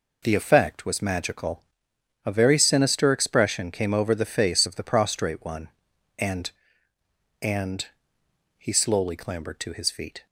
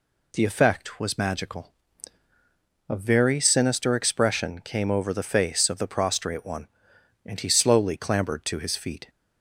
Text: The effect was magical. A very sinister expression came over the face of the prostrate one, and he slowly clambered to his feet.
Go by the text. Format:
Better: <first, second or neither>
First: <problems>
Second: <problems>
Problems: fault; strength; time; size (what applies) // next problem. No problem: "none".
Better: second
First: says "and" twice; at 7.4 s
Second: none